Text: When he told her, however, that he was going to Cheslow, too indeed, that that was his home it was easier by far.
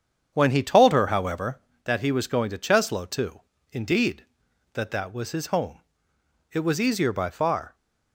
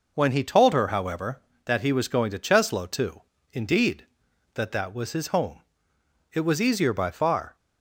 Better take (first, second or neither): second